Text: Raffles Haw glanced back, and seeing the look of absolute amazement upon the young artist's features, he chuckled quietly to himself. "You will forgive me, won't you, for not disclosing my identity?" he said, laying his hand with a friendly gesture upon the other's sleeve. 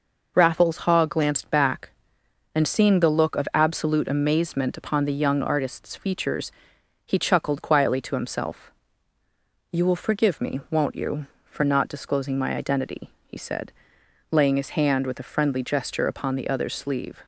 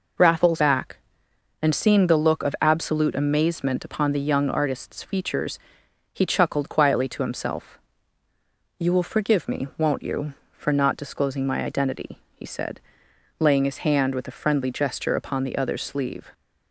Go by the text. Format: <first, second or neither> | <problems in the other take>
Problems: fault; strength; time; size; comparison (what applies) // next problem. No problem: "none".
first | skips "Haw glanced"; at 0.5 s